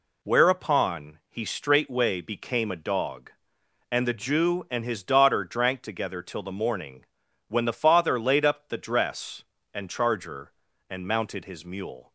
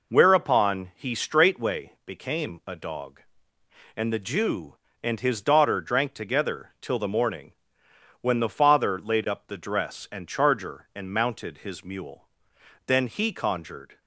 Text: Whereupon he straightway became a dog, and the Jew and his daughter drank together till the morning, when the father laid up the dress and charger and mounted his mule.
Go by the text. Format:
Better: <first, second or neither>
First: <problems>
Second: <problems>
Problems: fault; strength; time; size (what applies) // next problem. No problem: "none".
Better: first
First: none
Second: goes on to say "Then he conjured"; noticeable; from 12.8 s on; 1.1 s long